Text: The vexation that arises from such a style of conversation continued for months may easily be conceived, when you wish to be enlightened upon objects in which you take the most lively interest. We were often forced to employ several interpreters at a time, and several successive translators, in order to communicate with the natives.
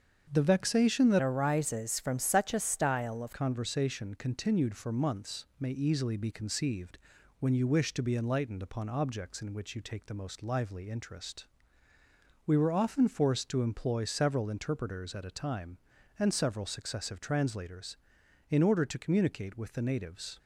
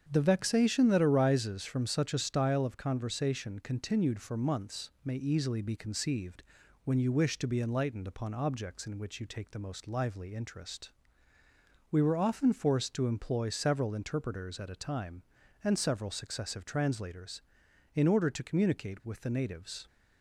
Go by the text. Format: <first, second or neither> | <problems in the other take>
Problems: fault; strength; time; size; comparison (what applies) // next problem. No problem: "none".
second | starts louder than the rest; strong; until 1.3 s; 7.5 dB; strong in the second // changes voice from "arises" to "of"; from 1.1 to 3.3 s; 2.2 s long